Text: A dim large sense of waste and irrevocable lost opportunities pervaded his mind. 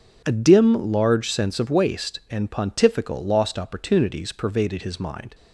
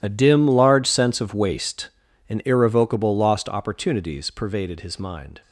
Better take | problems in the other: second | starts louder than the rest; until 1.2 s; 6.5 dB // says "pontifical" for "irrevocable"; at 2.4 s

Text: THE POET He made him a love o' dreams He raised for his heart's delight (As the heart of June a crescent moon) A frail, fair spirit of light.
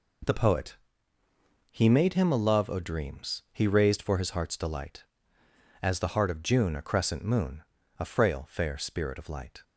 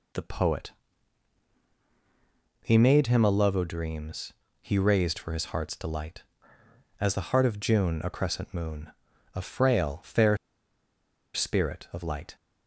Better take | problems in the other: first | pauses between "POET" and "He"; strong; at 0.7 s; 1.8 s long; noticeable in the first // pauses between "dreams" and "He"; slight; at 4.3 s; 0.28 s long // pauses between "fair" and "spirit"; noticeable; at 10.3 s; 0.97 s long

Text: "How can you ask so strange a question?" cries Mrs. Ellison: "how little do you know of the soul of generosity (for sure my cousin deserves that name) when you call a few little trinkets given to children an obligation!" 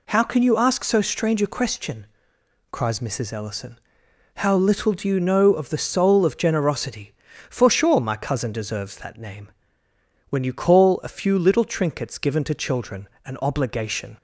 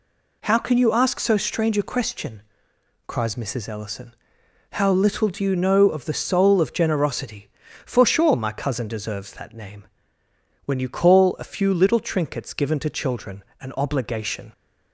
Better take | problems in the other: neither | pauses between "children" and "an"; slight; the same in both

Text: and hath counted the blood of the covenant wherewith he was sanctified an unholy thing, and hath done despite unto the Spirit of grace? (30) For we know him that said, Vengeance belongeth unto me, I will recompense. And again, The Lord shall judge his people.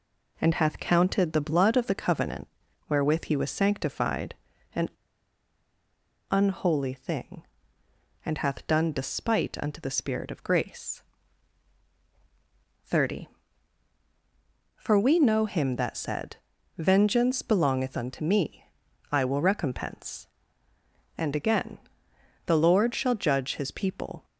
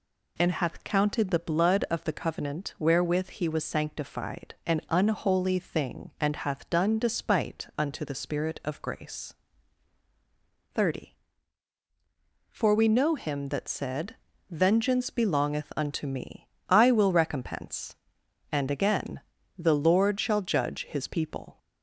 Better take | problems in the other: second | pauses between "covenant" and "wherewith"; at 2.4 s; 0.40 s long // pauses between "sanctified" and "an"; at 4.3 s; 0.40 s long // pauses between "an" and "unholy"; strong; at 4.8 s; 1.4 s long

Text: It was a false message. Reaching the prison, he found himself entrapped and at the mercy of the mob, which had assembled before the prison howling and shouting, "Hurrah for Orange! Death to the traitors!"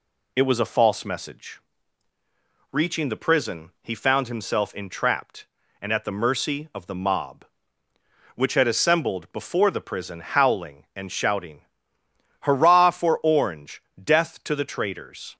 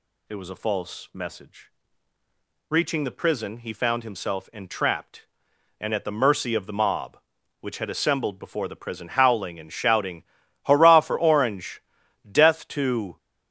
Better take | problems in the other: first | stops before "the traitors"; at 13.1 s

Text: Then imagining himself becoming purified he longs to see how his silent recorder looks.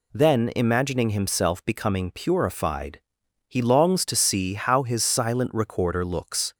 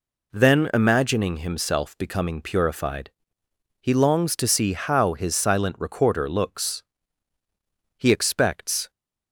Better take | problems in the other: first | pauses between "purified" and "he"; noticeable; at 3.1 s; 0.70 s long; noticeable in the first // goes on to say "He expects"; noticeable; from 7.9 s on; 0.94 s long

